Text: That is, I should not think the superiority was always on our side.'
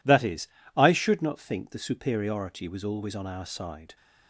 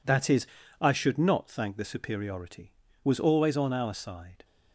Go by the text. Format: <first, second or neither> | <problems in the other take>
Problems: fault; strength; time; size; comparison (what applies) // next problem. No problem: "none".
first | says "thank" for "think"; at 1.5 s